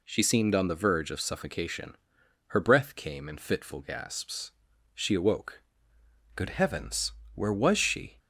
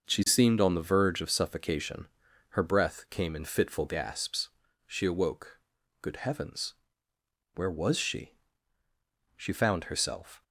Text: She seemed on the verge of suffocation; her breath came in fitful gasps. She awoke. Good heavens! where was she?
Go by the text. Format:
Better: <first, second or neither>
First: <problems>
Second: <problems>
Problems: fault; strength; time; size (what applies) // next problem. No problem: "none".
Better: first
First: none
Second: goes on to say "She found herself"; noticeable; from 9.3 s on; 1.0 s long